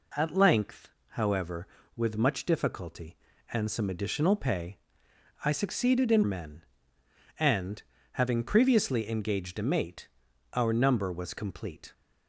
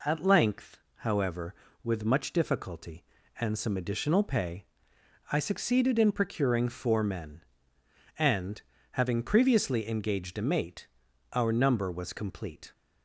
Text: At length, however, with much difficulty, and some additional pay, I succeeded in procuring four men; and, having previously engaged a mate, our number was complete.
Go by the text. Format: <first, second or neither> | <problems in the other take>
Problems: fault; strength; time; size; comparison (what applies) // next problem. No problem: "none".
second | skips "procuring four"; at 6.2 s